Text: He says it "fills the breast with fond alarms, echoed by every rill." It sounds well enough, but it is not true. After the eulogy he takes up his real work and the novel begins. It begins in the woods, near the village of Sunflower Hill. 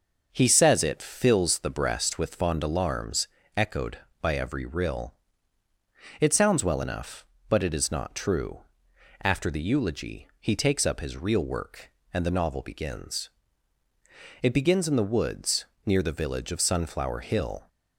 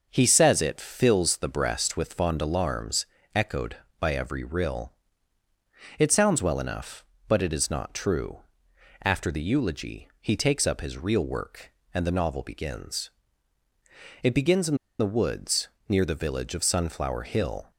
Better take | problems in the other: first | pauses between "in" and "the"; slight; at 14.7 s; 0.23 s long

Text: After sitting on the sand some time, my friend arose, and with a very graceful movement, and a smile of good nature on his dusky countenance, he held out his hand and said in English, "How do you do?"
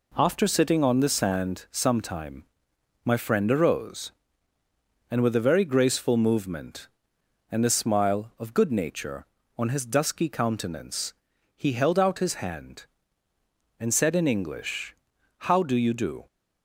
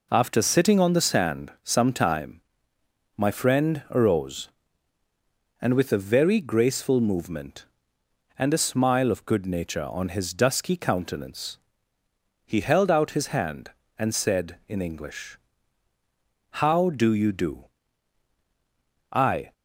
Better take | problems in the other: first | goes on to say "I"; slight; from 19.1 s on; 0.40 s long

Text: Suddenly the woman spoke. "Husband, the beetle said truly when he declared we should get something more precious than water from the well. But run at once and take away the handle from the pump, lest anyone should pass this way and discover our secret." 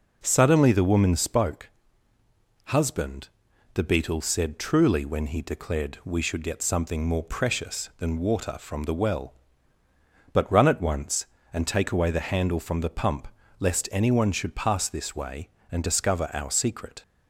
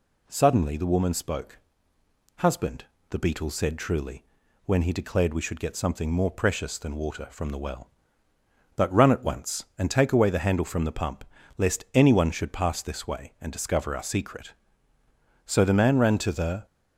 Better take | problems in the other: first | pauses between "truly" and "when"; at 4.2 s; 0.42 s long // goes on to say "So the man ran to the"; noticeable; from 15.4 s on; 1.2 s long

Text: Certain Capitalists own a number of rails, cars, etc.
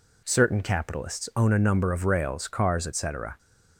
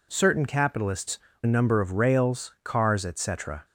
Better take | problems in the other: first | skips "own"; at 1.3 s

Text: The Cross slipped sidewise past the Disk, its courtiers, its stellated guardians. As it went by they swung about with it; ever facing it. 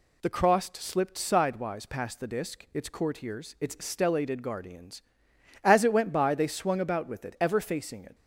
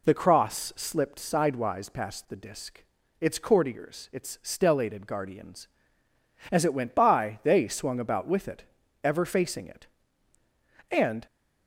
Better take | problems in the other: first | goes on to say "And"; slight; from 10.9 s on; 0.34 s long

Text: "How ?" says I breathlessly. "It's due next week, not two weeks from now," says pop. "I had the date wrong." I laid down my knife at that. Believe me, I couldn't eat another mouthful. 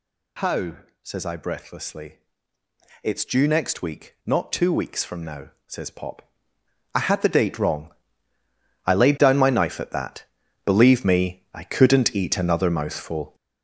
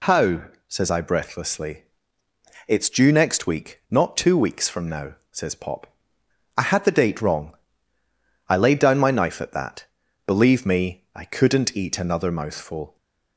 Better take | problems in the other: second | gets louder; strong; throughout; 10 dB

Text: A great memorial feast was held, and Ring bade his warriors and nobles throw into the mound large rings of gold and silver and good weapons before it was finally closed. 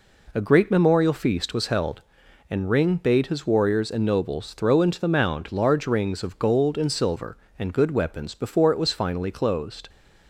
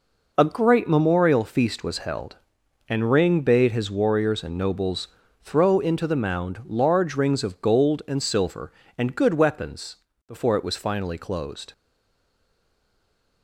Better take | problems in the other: first | pauses between "nobles" and "throw"; slight; at 5.0 s; 0.34 s long // pauses between "weapons" and "before"; slight; at 9.9 s; 0.32 s long // stays silent after the last word; noticeable; from 11.7 s on; 1.7 s long

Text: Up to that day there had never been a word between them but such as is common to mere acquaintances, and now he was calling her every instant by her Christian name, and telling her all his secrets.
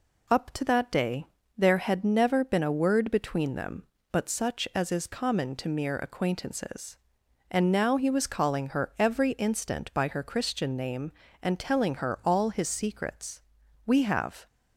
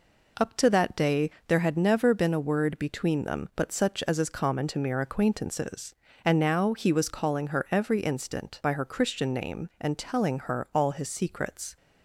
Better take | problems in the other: second | pauses between "day" and "there"; slight; at 1.2 s; 0.32 s long; slight in the second // goes on to say "We have"; from 13.8 s on; 0.60 s long

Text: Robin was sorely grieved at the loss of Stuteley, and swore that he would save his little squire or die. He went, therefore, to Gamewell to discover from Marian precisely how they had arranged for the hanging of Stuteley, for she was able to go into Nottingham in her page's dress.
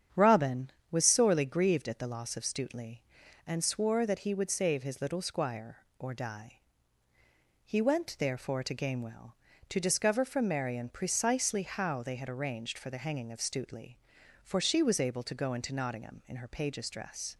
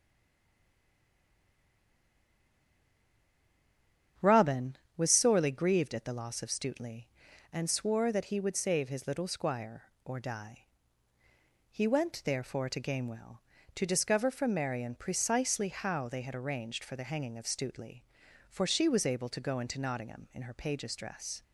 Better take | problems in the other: first | stays silent before the first word; strong; until 4.1 s; 4.1 s long // starts louder than the rest; strong; until 5.4 s; 8.5 dB; strong in the first

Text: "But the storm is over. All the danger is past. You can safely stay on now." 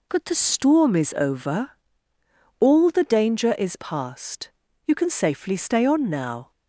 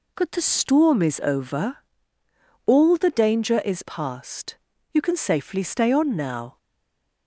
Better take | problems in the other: first | stays silent after the last word; slight; from 6.5 s on; 0.7 s long

